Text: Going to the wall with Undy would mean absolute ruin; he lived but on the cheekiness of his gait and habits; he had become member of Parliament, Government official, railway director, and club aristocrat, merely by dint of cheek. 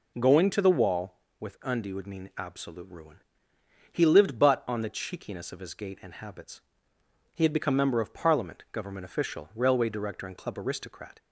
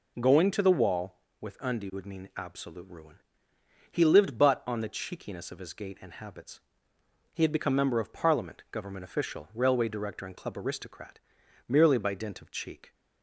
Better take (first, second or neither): second